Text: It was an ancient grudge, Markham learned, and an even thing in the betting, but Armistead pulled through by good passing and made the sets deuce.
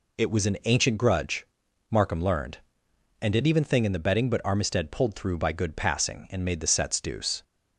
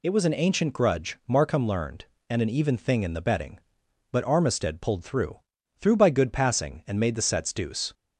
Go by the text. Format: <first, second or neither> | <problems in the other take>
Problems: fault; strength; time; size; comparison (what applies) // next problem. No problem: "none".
first | says "through" twice; at 5.7 s